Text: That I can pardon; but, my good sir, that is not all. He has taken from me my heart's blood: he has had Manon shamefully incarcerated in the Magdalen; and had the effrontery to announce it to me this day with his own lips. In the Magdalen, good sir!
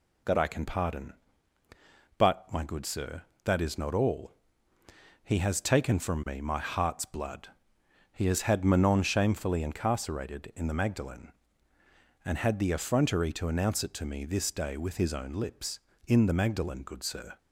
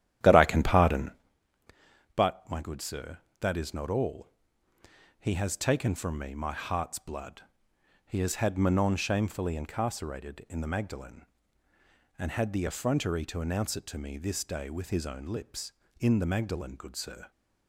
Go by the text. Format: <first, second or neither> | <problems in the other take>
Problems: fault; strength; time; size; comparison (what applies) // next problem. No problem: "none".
first | starts louder than the rest; strong; until 1.3 s; 11.5 dB